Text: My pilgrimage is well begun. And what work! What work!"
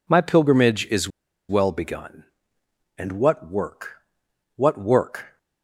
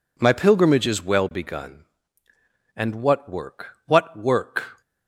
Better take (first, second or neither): second